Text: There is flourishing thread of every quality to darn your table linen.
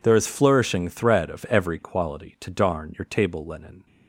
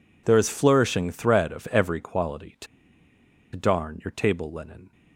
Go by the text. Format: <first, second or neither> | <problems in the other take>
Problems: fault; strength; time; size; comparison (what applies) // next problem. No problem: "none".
first | pauses between "to" and "darn"; noticeable; at 2.6 s; 0.88 s long